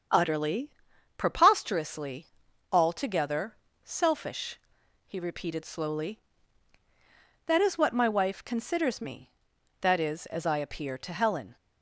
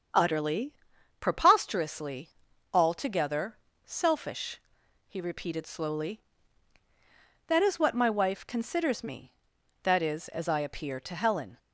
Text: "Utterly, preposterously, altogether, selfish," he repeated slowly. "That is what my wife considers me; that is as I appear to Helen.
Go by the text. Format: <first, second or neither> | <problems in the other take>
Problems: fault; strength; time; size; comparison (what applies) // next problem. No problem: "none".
neither | starts louder than the rest; strong; the same in both